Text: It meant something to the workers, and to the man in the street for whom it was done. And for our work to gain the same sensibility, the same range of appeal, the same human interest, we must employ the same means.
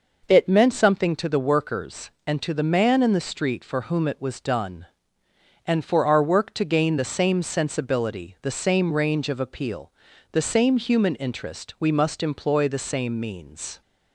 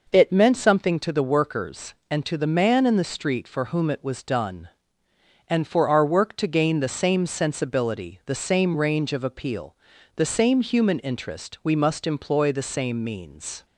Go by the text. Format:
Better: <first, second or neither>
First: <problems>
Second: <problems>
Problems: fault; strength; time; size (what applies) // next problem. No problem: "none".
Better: neither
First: none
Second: none